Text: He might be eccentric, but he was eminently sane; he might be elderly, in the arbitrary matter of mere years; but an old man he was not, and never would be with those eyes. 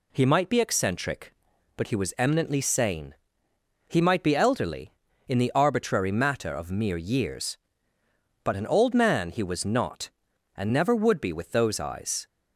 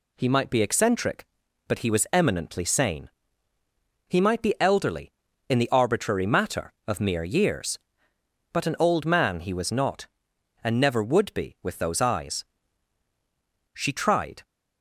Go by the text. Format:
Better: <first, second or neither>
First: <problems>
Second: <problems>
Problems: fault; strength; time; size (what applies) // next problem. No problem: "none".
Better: first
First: none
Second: goes on to say "She tried"; noticeable; from 13.7 s on; 0.70 s long